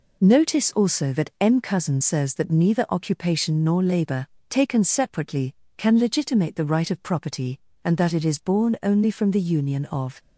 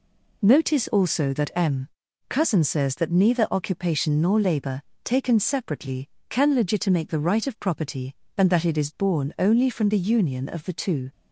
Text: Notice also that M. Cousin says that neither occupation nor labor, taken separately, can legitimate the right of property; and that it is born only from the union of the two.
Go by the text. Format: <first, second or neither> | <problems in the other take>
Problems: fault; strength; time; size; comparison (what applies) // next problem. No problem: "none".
second | stops before "the two"; at 10.1 s